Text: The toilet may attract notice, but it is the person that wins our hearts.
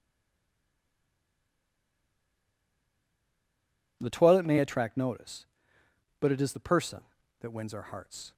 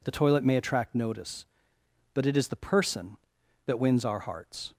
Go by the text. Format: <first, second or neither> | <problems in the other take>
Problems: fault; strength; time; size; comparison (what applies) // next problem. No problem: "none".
second | stays silent before the first word; strong; until 3.9 s; 3.9 s long